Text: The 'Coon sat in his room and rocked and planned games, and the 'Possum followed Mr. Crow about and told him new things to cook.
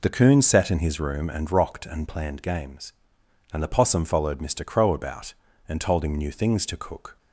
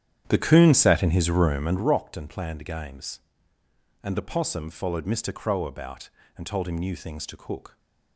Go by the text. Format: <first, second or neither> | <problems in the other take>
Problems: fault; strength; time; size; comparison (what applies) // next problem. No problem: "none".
first | starts louder than the rest; strong; until 2.0 s; 10 dB